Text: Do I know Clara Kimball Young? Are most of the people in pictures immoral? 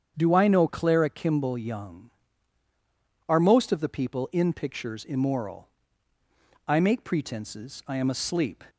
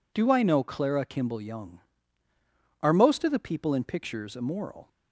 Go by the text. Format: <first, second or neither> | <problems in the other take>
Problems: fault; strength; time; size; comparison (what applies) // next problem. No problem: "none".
second | starts louder than the rest; strong; until 1.1 s; 7.5 dB // goes on to say "I make pretenses I am asleep"; strong; from 6.6 s on; 1.9 s long